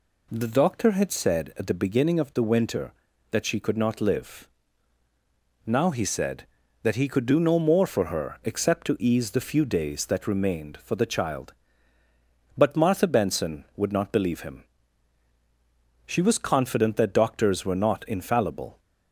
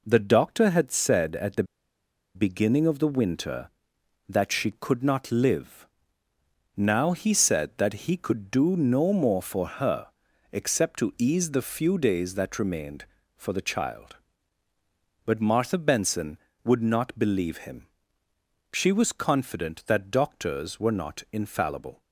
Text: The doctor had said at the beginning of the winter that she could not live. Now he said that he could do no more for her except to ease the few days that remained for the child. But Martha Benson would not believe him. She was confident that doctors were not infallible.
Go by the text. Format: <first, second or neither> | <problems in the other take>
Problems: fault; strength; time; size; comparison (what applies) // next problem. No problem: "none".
first | pauses between "the" and "beginning"; noticeable; at 1.6 s; 0.71 s long // pauses between "her" and "except"; noticeable; at 10.0 s; 0.46 s long